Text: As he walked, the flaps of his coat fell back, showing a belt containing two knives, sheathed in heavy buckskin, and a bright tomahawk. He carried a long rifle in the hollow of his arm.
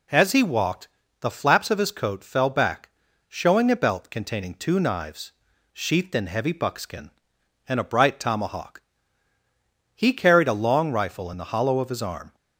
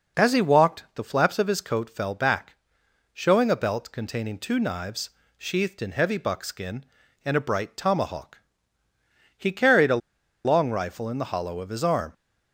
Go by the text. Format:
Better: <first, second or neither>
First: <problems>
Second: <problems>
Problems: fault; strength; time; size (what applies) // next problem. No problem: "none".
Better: first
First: none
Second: pauses between "a" and "long"; noticeable; at 10.0 s; 0.46 s long